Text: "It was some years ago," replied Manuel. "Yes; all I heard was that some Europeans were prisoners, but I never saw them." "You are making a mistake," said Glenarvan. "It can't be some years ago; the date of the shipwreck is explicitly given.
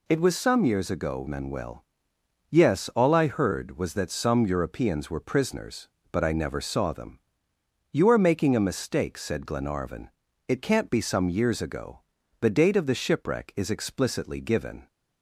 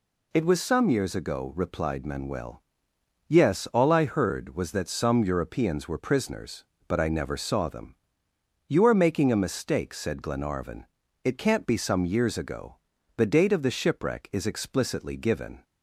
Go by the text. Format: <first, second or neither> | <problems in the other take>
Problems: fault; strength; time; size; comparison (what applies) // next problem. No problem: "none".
second | skips "replied"; at 1.2 s